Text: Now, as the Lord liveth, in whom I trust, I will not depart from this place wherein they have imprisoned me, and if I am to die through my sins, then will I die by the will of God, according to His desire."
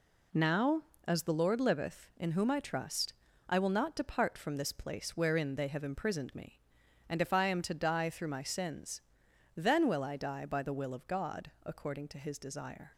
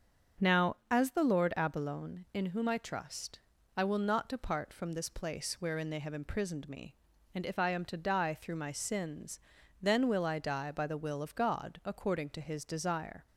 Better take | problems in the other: first | starts louder than the rest; strong; until 1.5 s; 7 dB // says "abalone" for "liveth"; at 1.5 s

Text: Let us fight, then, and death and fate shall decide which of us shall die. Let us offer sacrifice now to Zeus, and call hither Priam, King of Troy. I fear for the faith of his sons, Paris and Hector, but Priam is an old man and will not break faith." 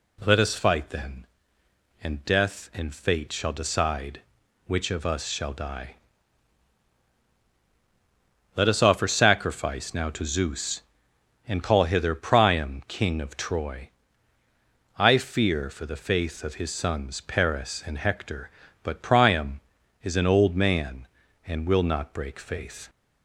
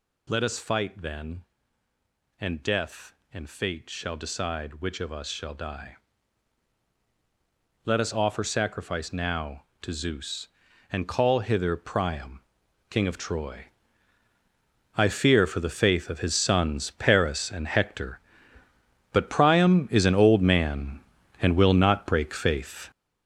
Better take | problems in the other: first | gets louder; strong; throughout; 9.5 dB

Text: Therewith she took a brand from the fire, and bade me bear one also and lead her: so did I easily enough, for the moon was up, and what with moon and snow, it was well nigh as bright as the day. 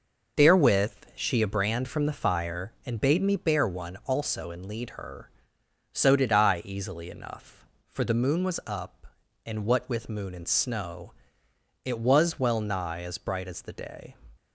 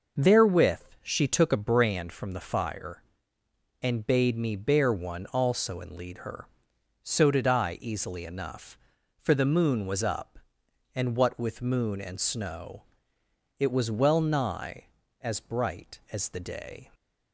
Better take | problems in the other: second | pauses between "Therewith" and "she"; slight; at 0.9 s; 0.20 s long; slight in the second // skips "took"; at 1.4 s

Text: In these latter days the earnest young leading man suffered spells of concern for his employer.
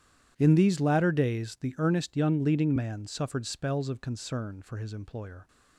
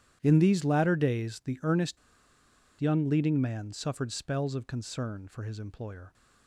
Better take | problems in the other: first | starts louder than the rest; strong; until 1.2 s; 10.5 dB; strong in the first // pauses between "earnest" and "young"; noticeable; at 1.9 s; 0.83 s long

